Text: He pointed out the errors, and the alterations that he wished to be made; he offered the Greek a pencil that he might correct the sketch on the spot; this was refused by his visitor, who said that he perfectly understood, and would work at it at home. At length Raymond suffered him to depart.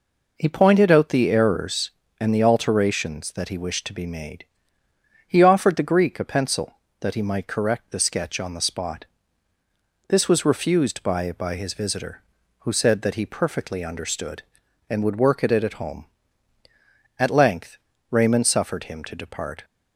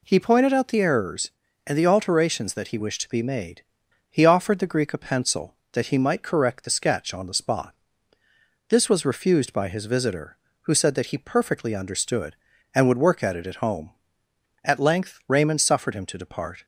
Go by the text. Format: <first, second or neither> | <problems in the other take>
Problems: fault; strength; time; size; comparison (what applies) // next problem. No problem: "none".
second | says "by" twice; at 11.3 s // pauses between "length" and "Raymond"; slight; at 17.7 s; 0.34 s long